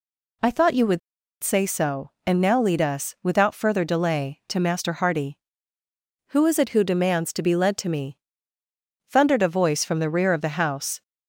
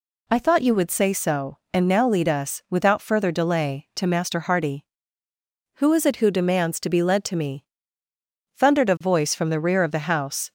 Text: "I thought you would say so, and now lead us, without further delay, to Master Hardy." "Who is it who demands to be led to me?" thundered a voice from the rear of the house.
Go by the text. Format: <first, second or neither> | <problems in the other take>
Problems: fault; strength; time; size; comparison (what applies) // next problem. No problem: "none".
second | pauses between "would" and "say"; at 0.9 s; 0.44 s long